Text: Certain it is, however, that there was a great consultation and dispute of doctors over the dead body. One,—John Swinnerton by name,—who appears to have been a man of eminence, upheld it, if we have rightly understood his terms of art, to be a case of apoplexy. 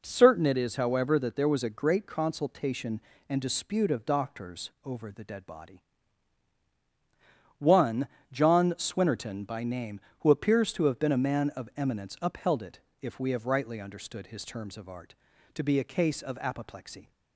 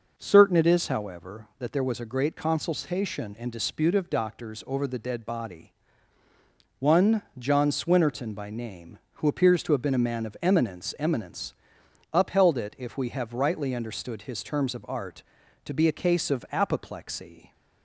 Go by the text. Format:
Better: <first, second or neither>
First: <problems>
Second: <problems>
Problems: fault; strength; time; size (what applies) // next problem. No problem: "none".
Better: first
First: none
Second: says "eminence" twice; at 10.9 s